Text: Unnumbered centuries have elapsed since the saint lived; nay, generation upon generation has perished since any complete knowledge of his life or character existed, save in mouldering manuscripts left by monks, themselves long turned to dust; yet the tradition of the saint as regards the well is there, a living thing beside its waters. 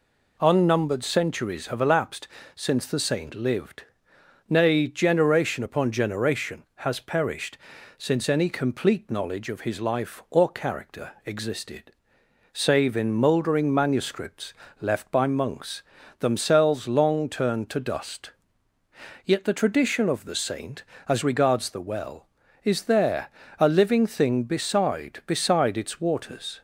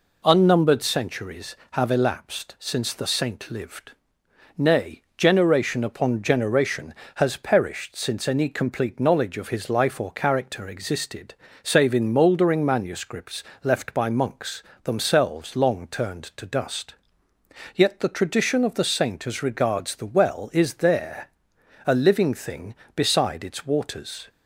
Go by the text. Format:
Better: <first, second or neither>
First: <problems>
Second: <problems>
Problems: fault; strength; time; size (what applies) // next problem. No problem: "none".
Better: second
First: pauses between "elapsed" and "since"; slight; at 2.2 s; 0.28 s long // pauses between "perished" and "since"; at 7.5 s; 0.40 s long // pauses between "manuscripts" and "left"; slight; at 14.5 s; 0.28 s long // says "beside" twice; at 25.2 s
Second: pauses between "manuscripts" and "left"; slight; at 13.4 s; 0.22 s long